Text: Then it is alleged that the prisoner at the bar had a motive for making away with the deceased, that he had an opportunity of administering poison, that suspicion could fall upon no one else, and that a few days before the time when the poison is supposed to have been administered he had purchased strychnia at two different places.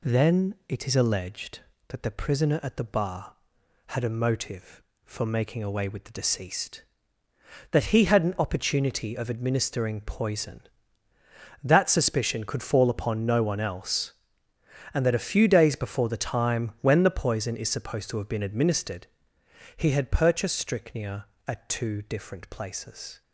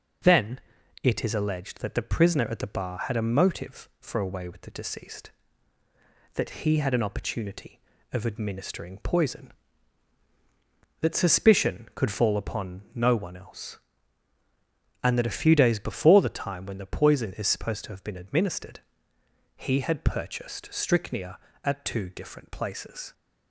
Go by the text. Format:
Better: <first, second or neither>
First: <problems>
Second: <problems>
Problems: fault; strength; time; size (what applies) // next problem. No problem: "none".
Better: first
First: pauses between "administered" and "he"; noticeable; at 19.0 s; 0.70 s long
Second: pauses between "Then" and "it"; at 0.6 s; 0.42 s long // skips "making"; at 4.1 s // pauses between "administered" and "he"; noticeable; at 18.7 s; 0.76 s long